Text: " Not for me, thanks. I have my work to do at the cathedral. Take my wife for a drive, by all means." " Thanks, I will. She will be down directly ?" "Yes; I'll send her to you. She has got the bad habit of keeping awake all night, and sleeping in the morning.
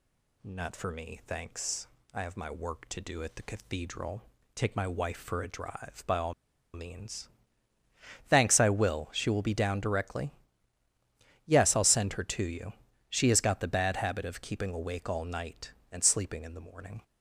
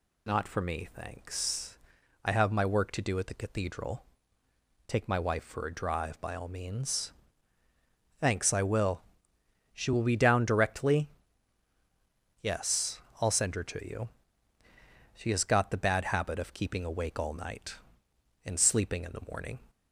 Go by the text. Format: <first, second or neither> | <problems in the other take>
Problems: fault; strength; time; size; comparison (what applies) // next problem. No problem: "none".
second | pauses between "all" and "means"; at 6.3 s; 0.41 s long